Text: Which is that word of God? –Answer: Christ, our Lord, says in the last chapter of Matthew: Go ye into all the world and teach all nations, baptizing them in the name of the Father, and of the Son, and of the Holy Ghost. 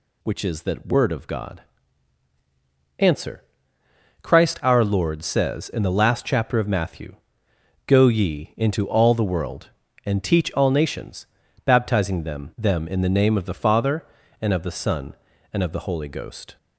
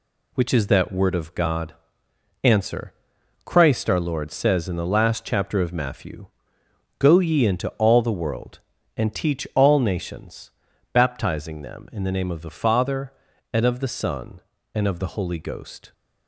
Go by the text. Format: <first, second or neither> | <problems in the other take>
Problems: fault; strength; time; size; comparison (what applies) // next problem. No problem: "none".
second | says "them" twice; at 12.5 s